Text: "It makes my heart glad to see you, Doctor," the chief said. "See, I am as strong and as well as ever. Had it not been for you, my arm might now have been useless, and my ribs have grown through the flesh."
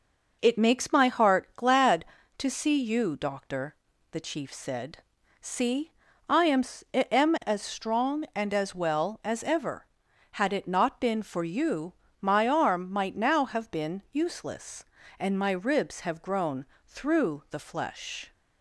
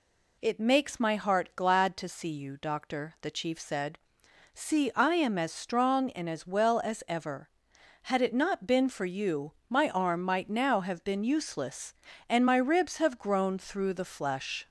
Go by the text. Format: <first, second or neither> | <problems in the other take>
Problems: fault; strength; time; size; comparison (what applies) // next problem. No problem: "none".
second | says "am" twice; at 6.9 s // pauses between "grown" and "through"; slight; at 16.6 s; 0.22 s long